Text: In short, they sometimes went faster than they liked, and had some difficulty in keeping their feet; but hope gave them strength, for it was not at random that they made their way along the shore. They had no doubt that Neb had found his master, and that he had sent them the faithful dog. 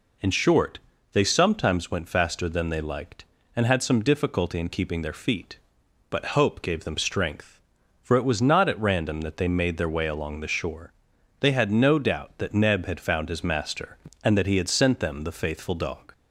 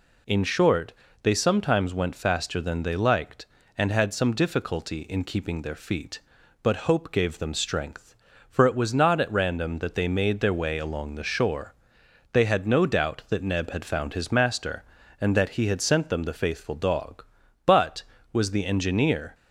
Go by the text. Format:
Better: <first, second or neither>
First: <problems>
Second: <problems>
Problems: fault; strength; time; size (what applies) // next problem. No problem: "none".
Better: first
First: none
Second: goes on to say "But was the engineer"; strong; from 17.6 s on; 1.6 s long